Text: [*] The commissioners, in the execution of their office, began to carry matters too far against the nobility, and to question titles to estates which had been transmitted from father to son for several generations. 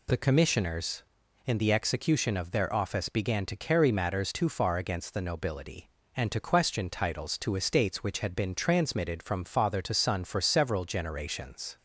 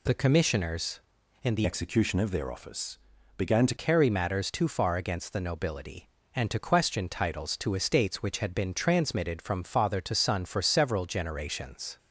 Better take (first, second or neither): first